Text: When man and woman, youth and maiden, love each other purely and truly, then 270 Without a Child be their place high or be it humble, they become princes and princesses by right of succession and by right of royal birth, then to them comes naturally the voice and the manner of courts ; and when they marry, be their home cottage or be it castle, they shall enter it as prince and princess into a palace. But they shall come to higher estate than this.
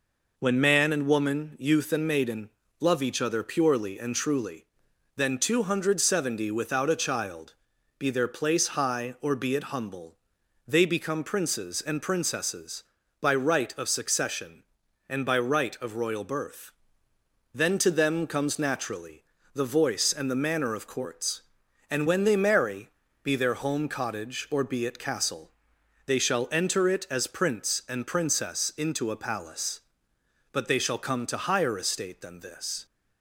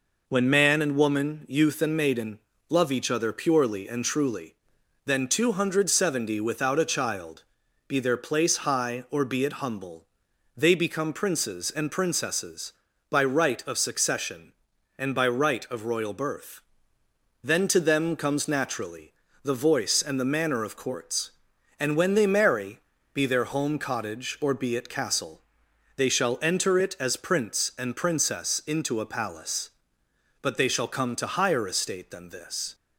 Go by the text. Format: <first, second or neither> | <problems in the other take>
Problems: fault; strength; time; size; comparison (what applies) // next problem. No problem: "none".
neither | pauses between "Child" and "be"; the same in both // pauses between "naturally" and "the"; slight; the same in both